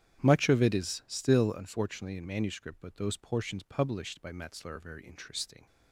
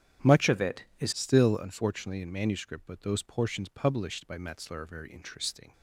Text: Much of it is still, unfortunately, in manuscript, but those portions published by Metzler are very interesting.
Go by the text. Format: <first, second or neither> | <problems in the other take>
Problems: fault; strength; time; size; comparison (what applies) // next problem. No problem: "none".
first | starts louder than the rest; strong; until 1.3 s; 9.5 dB; strong in the first // changes voice from "of" to "is"; from 0.4 to 1.1 s; 0.7 s long